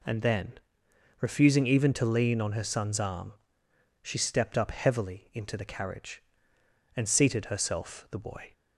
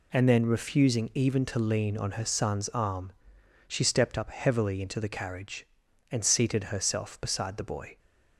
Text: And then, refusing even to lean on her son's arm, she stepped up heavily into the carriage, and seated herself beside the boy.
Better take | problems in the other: second | skips "beside"; at 8.0 s

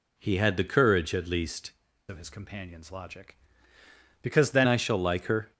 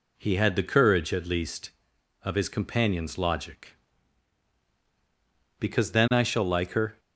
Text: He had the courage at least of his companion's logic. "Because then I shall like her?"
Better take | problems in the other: second | changes voice from "of" to "then"; from 2.0 to 4.6 s; 2.6 s long

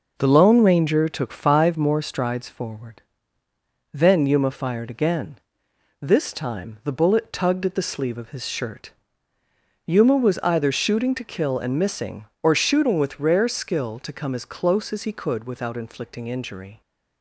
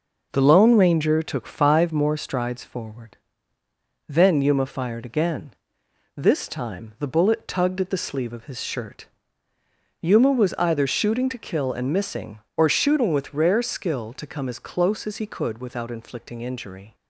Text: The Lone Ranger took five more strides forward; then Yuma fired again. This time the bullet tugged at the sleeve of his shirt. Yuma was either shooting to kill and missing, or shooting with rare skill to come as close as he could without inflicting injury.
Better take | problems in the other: neither | none

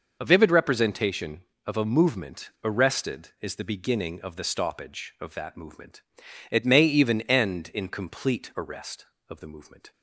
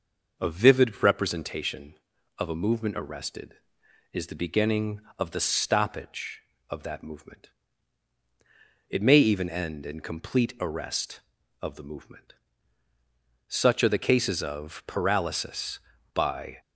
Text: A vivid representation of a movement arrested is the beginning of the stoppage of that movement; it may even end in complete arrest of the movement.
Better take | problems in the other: first | goes on to say "Such are the cases of paralysis by"; strong; from 13.4 s on; 3.1 s long

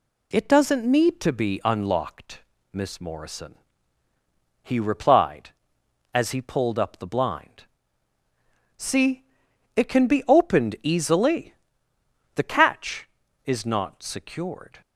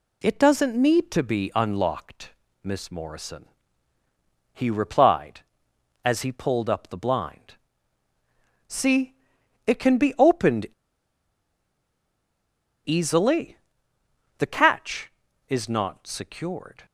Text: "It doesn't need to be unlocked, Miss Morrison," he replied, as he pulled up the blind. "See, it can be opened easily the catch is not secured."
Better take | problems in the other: first | pauses between "opened" and "easily"; strong; at 10.6 s; 2.2 s long // pauses between "easily" and "the"; noticeable; at 13.5 s; 0.82 s long; noticeable in the first

